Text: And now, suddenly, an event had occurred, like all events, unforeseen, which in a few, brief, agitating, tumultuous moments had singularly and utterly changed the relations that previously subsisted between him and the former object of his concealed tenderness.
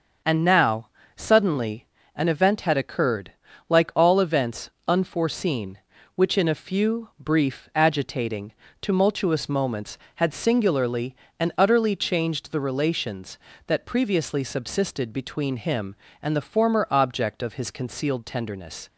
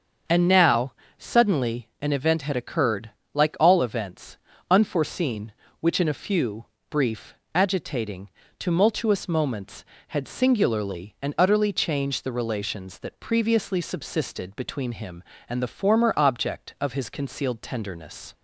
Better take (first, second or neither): neither